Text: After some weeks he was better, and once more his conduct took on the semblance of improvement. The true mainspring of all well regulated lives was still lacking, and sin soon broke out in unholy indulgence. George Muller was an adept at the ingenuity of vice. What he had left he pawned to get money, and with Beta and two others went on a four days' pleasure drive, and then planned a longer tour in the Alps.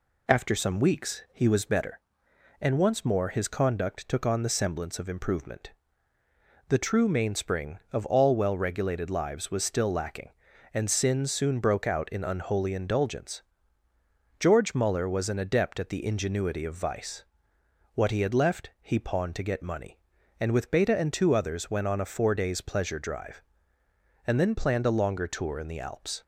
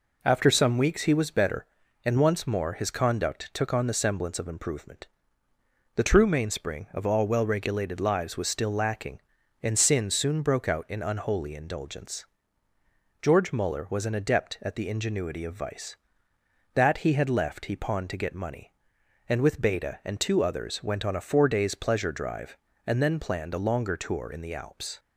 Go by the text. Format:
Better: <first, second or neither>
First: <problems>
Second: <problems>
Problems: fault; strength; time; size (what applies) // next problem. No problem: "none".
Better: first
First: none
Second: says "That" for "What"; at 16.7 s